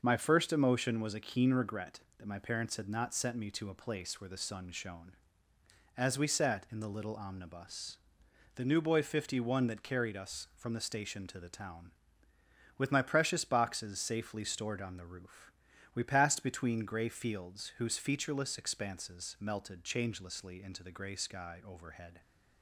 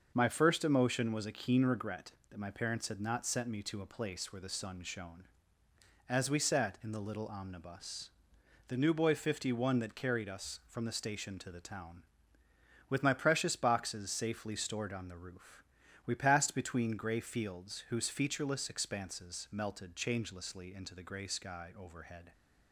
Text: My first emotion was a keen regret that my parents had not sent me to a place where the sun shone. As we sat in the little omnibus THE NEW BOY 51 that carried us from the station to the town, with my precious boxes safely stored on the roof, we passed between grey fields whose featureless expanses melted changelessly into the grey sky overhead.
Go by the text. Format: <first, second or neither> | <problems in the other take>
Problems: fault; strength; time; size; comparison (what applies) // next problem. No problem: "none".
neither | starts louder than the rest; noticeable; the same in both // pauses between "omnibus" and "THE"; noticeable; the same in both